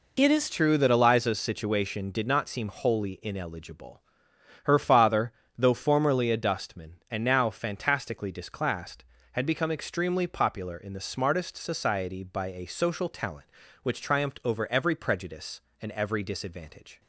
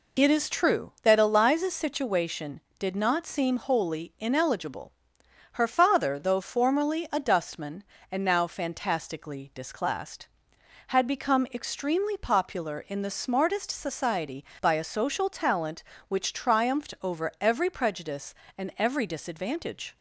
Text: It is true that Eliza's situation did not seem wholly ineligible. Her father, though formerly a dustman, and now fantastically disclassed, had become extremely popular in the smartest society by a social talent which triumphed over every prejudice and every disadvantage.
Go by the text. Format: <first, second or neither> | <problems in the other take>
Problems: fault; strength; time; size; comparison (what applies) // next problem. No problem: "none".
second | changes voice at "true"; from 0.4 s on; 16.6 s long